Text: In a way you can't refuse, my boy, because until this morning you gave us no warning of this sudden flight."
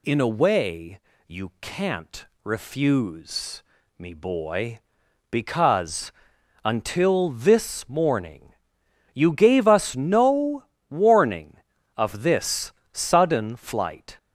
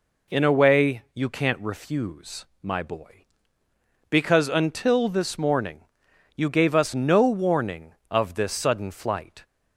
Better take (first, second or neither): second